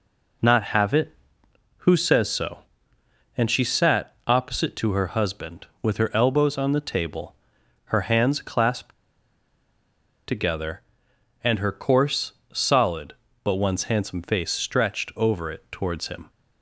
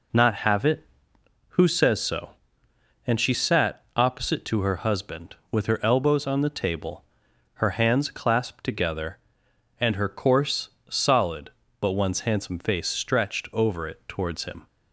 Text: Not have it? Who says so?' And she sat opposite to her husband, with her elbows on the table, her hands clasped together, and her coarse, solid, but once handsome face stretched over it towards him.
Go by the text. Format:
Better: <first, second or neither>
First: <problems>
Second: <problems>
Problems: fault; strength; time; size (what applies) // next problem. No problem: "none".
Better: second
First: pauses between "clasped" and "together"; strong; at 8.9 s; 1.3 s long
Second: none